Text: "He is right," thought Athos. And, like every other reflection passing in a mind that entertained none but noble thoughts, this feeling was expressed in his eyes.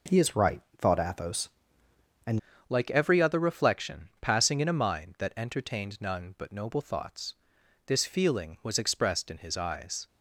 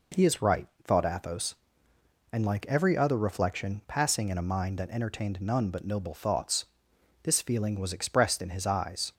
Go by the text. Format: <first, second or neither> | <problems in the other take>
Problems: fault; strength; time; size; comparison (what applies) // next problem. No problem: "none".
second | changes voice at "like"; from 2.6 s on; 7.4 s long